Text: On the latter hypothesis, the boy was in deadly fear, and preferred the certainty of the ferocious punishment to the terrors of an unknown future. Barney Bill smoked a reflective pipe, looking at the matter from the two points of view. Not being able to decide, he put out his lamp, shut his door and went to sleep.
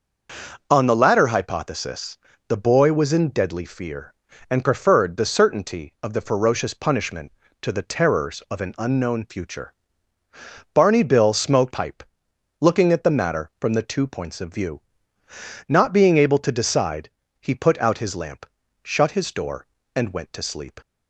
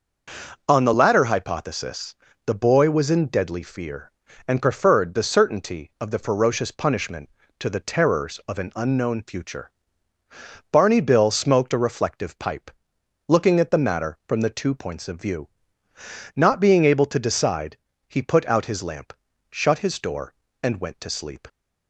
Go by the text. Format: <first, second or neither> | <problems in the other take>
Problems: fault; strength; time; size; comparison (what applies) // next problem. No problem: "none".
second | skips "a reflective"; at 11.7 s